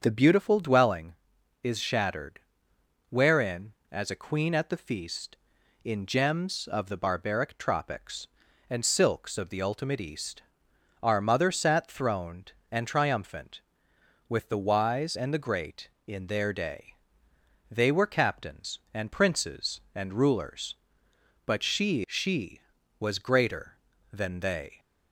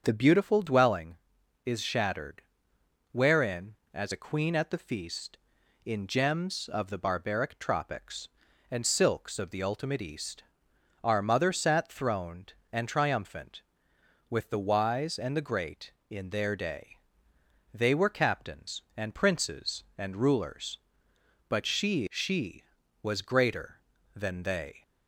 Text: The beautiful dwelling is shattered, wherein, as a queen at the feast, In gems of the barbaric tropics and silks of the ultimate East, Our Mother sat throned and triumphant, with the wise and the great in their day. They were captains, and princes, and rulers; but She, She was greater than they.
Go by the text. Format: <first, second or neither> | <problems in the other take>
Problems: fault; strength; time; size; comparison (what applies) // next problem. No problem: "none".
neither | starts louder than the rest; the same in both